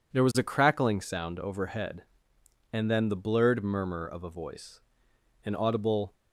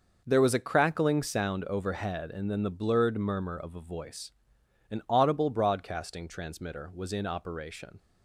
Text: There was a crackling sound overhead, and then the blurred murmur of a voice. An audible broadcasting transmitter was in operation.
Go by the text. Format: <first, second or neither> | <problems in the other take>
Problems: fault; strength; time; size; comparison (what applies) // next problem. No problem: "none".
second | stops before "broadcasting transmitter was in operation"; at 6.1 s